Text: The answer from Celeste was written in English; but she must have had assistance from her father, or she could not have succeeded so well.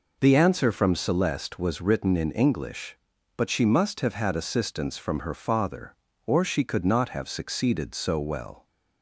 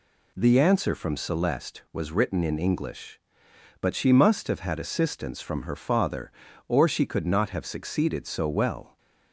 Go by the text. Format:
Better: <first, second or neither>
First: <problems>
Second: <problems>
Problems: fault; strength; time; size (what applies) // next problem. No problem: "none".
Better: neither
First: none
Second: none